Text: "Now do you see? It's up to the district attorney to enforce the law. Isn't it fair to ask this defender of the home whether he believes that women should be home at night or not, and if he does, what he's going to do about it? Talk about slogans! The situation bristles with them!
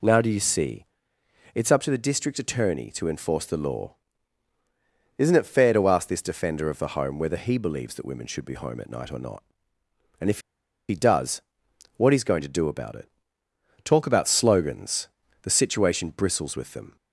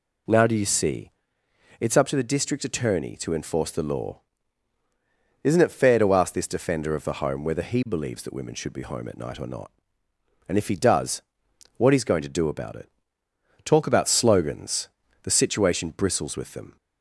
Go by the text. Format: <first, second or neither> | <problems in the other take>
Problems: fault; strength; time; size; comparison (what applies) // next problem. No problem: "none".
second | pauses between "if" and "he"; noticeable; at 10.4 s; 0.48 s long